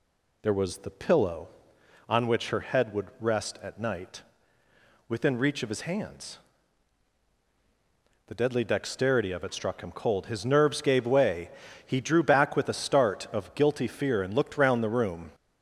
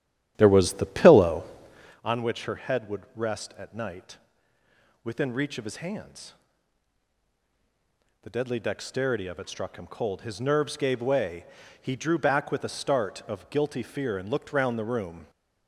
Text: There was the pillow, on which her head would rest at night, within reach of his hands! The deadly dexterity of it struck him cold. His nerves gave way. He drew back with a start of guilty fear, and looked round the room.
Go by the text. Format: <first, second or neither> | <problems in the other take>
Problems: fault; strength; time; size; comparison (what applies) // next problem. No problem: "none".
first | starts louder than the rest; strong; until 2.0 s; 12 dB